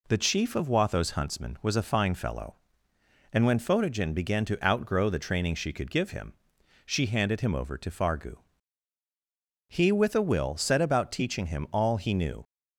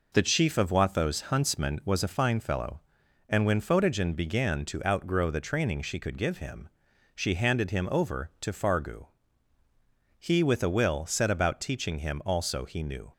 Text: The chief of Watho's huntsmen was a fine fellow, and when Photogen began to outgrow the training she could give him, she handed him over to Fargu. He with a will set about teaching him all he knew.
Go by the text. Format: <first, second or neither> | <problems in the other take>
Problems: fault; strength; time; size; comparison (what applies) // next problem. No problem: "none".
first | says "also" for "all"; at 12.2 s